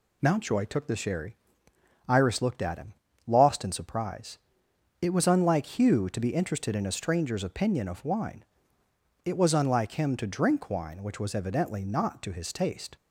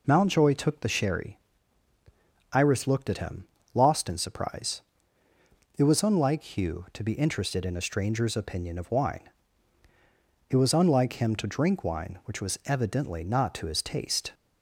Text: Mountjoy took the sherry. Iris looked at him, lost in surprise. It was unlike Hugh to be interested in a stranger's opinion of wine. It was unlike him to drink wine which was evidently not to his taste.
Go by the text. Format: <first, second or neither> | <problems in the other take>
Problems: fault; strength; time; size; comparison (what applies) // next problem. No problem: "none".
neither | none